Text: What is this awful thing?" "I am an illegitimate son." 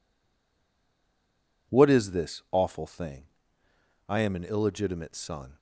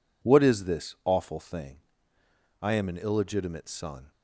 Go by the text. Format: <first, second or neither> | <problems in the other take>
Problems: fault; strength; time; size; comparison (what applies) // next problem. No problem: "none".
second | stays silent before the first word; noticeable; until 1.6 s; 1.6 s long